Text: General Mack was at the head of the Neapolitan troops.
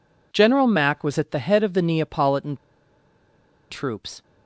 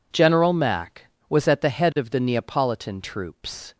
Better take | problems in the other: second | pauses between "Neapolitan" and "troops"; at 2.5 s; 1.1 s long

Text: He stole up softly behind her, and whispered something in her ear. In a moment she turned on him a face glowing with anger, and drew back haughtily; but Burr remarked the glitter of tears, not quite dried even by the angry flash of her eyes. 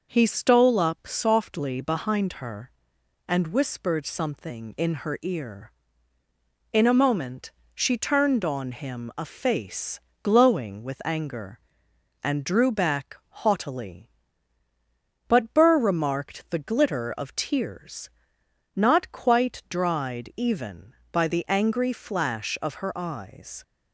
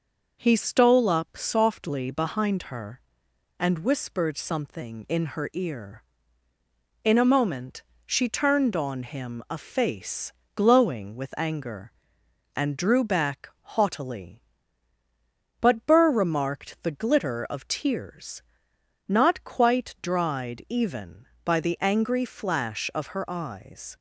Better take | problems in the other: neither | pauses between "moment" and "she"; slight; the same in both // pauses between "face" and "glowing"; slight; the same in both // pauses between "back" and "haughtily"; slight; the same in both

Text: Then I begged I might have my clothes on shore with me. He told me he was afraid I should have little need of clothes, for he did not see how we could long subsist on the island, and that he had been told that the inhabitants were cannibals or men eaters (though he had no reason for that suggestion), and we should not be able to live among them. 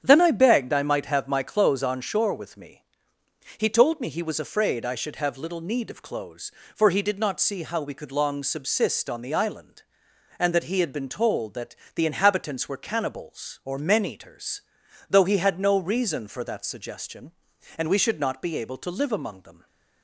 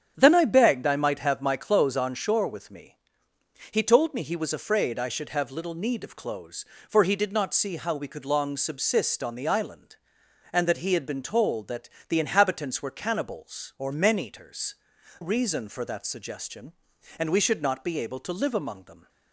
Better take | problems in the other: first | starts louder than the rest; strong; until 1.1 s; 8 dB; strong in the first // pauses between "that" and "the"; slight; at 11.8 s; 0.20 s long; slight in the first // skips "though he had no"; at 14.9 s

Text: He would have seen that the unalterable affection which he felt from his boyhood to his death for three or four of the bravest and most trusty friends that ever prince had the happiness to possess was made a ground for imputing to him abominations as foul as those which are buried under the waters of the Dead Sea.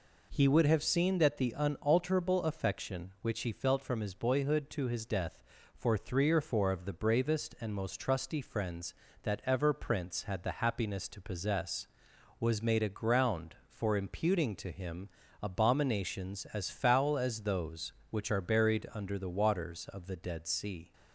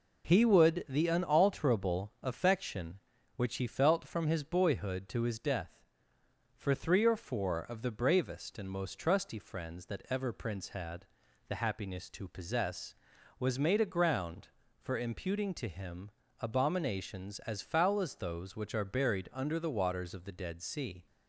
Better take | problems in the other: first | skips "have seen that"; at 0.8 s // pauses between "had" and "the"; at 11.0 s; 0.40 s long // pauses between "him" and "abominations"; slight; at 16.0 s; 0.30 s long; slight in the first

